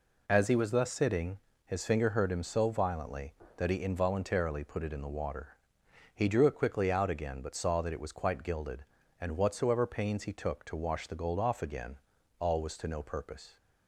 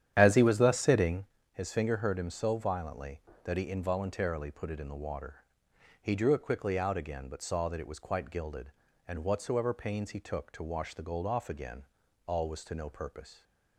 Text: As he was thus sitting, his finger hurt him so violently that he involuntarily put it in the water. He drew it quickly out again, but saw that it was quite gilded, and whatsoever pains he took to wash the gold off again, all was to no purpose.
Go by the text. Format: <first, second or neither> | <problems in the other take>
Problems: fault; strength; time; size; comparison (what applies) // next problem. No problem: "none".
first | starts louder than the rest; strong; until 1.3 s; 10 dB